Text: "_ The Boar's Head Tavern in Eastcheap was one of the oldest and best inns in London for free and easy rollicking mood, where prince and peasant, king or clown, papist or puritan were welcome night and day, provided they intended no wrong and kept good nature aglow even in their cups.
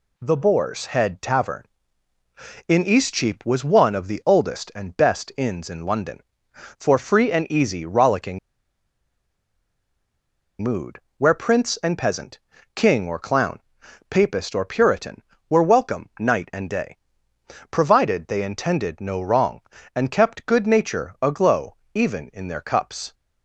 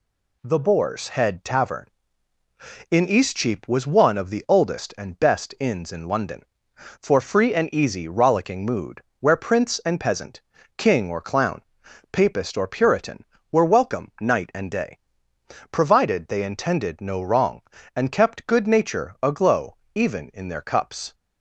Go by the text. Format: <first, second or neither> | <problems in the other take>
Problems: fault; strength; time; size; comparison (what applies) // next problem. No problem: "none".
second | pauses between "rollicking" and "mood"; strong; at 8.3 s; 2.2 s long // pauses between "aglow" and "even"; slight; at 21.7 s; 0.20 s long; slight in the second